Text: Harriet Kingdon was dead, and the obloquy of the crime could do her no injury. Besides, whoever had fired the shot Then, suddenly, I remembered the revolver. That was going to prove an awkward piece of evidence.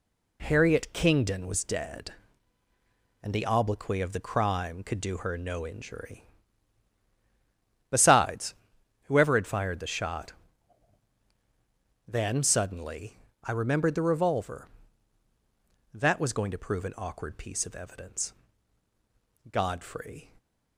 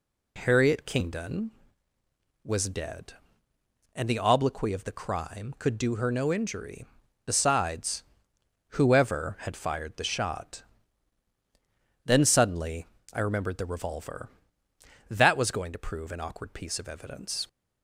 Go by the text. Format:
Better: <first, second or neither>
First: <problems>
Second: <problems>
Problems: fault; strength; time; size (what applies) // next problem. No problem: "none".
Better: second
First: pauses between "shot" and "Then"; strong; at 10.3 s; 1.7 s long // goes on to say "Godfrey"; noticeable; from 19.5 s on; 0.80 s long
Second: pauses between "shot" and "Then"; strong; at 10.6 s; 1.4 s long